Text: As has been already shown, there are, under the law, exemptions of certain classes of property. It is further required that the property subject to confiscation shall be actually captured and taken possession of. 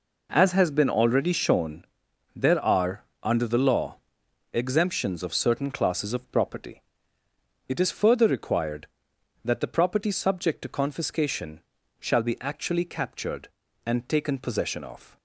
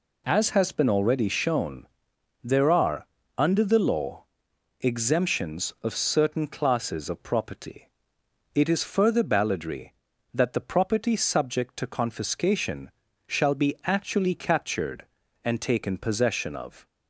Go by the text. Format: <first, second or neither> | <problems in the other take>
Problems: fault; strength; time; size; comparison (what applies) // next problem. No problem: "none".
first | says "balladry" for "required"; at 9.2 s // pauses between "confiscation" and "shall"; slight; at 12.8 s; 0.36 s long; also in the first